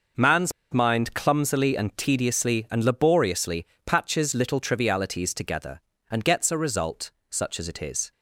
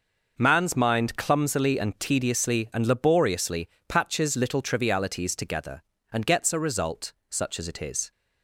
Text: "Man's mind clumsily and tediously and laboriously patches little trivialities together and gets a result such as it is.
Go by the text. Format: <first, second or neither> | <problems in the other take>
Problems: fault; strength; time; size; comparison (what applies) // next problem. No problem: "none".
second | pauses between "Man's" and "mind"; slight; at 0.5 s; 0.20 s long // pauses between "laboriously" and "patches"; slight; at 3.6 s; 0.20 s long; slight in the second // pauses between "result" and "such"; slight; at 7.1 s; 0.18 s long; slight in the second